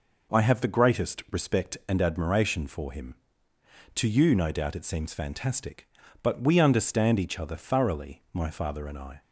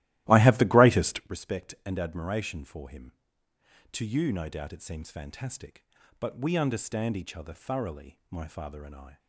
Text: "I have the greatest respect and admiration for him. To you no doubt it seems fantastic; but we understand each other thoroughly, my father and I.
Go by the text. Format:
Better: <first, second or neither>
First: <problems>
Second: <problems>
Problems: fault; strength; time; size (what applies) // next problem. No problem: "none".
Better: first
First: none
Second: starts louder than the rest; strong; until 1.3 s; 16 dB